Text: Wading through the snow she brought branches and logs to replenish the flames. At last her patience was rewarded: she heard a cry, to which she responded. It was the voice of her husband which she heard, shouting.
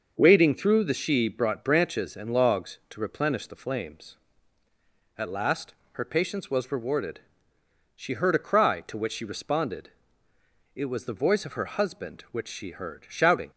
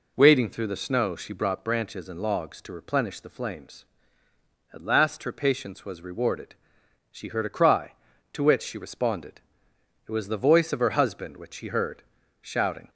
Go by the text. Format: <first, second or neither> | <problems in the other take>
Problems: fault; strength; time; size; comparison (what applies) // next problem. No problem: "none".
second | starts louder than the rest; noticeable; until 1.2 s; 6 dB // skips "snow"; at 0.9 s // pauses between "last" and "her"; slight; at 5.7 s; 0.18 s long